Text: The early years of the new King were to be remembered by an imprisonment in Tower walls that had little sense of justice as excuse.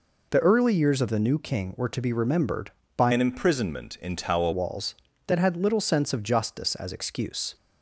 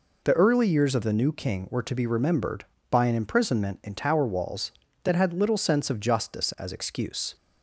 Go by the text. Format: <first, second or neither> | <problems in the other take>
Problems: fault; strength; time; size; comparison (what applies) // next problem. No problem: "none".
second | changes voice from "an" to "Tower"; from 3.1 to 4.5 s; 1.4 s long